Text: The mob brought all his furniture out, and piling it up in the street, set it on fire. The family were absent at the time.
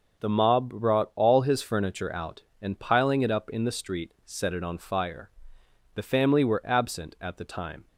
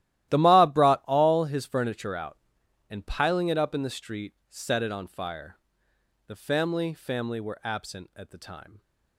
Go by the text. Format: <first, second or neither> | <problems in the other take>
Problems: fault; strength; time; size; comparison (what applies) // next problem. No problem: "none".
first | starts louder than the rest; strong; until 1.3 s; 14 dB // says "family" twice; at 6.9 s